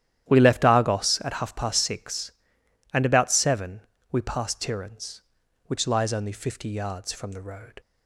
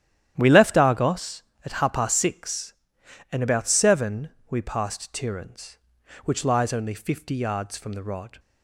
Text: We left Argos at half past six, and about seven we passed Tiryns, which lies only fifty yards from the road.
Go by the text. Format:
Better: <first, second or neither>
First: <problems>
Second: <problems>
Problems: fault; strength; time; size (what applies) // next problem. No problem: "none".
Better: first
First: starts louder than the rest; strong; until 1.3 s; 11.5 dB // pauses between "seven" and "we"; slight; at 3.8 s; 0.28 s long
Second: starts louder than the rest; strong; until 1.3 s; 11 dB // pauses between "seven" and "we"; slight; at 4.3 s; 0.18 s long // says "rod" for "road"; at 8.0 s